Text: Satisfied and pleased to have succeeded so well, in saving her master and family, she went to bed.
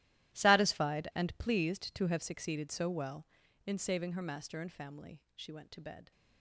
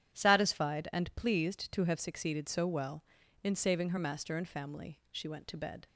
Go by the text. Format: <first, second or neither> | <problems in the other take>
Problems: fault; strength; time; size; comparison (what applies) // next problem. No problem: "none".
second | gets quieter; strong; throughout; 17.5 dB // starts louder than the rest; strong; until 1.4 s; 14.5 dB; strong in the second